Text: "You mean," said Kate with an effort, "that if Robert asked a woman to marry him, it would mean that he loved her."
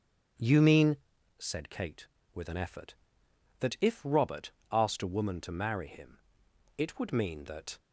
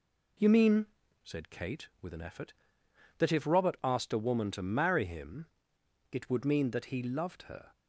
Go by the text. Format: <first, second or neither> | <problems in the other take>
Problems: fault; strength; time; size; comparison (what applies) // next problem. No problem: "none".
second | starts louder than the rest; strong; until 1.7 s; 8 dB // pauses between "Robert" and "asked"; slight; at 4.5 s; 0.20 s long // stops before "he loved her"; at 7.7 s